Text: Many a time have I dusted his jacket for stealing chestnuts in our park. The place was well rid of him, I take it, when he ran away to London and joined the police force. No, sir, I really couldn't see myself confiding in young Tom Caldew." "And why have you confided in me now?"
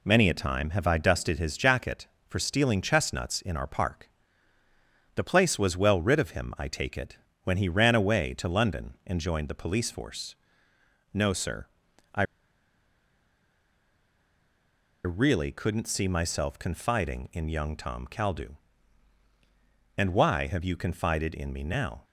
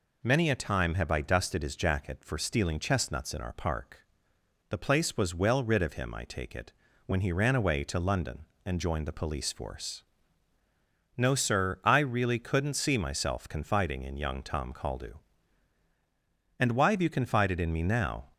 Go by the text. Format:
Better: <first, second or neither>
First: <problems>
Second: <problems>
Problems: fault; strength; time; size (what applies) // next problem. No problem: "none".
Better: second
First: pauses between "I" and "really"; strong; at 12.2 s; 2.8 s long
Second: none